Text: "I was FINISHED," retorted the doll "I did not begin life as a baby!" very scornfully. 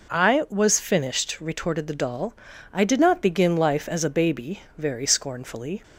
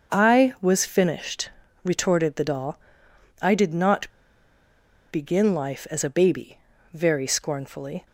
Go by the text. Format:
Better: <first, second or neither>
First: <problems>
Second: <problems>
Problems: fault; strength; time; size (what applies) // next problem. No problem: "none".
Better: first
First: pauses between "doll" and "I"; at 2.3 s; 0.40 s long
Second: starts louder than the rest; until 1.1 s; 6.5 dB // pauses between "doll" and "I"; noticeable; at 2.7 s; 0.62 s long // pauses between "not" and "begin"; at 4.0 s; 1.0 s long